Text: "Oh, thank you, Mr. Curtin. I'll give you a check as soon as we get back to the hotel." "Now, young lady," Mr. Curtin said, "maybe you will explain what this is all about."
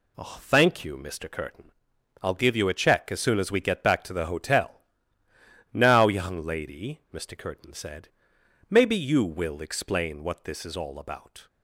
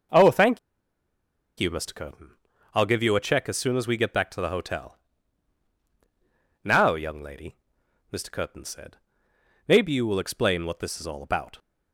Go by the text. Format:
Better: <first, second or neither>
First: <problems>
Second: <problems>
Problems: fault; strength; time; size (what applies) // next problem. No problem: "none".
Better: first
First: none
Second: pauses between "thank" and "you"; at 0.5 s; 1.0 s long